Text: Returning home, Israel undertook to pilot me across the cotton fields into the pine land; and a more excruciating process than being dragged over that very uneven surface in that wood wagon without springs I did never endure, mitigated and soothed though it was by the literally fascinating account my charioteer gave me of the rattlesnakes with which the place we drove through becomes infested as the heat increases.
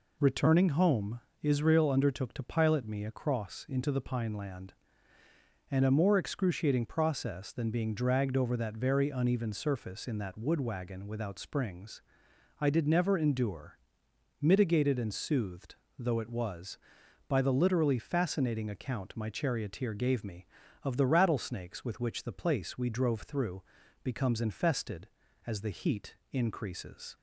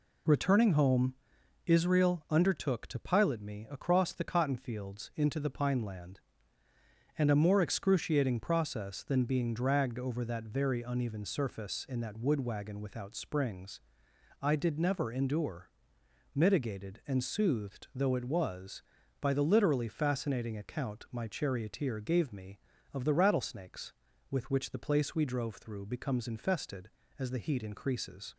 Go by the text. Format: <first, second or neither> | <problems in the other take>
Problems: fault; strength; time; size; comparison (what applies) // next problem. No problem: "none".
second | skips "the cotton fields"; at 3.6 s // pauses between "springs" and "I"; noticeable; at 12.0 s; 0.58 s long; noticeable in the second // pauses between "soothed" and "though"; slight; at 15.7 s; 0.24 s long // pauses between "through" and "becomes"; at 23.6 s; 0.40 s long // pauses between "heat" and "increases"; slight; at 26.1 s; 0.16 s long